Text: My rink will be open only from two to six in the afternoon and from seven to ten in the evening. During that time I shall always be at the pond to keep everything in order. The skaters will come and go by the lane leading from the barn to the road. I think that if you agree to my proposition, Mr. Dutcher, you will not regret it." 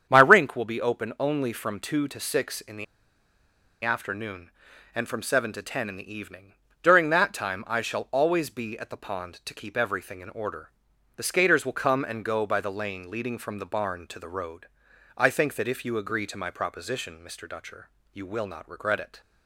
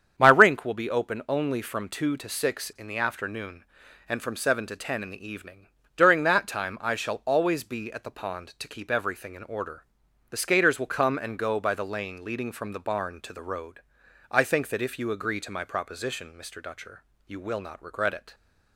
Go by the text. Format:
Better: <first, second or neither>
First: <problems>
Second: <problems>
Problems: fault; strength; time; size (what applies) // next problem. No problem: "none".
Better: second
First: starts louder than the rest; strong; until 1.1 s; 8 dB // pauses between "the" and "afternoon"; at 2.8 s; 0.99 s long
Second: starts louder than the rest; strong; until 1.1 s; 8 dB